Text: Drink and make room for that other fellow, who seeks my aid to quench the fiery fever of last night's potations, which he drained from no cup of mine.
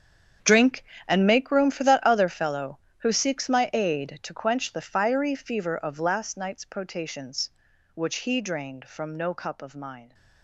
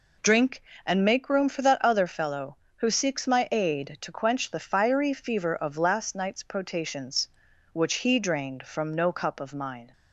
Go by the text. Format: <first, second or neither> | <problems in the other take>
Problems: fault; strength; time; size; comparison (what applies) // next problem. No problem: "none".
second | gets quieter; strong; throughout; 14 dB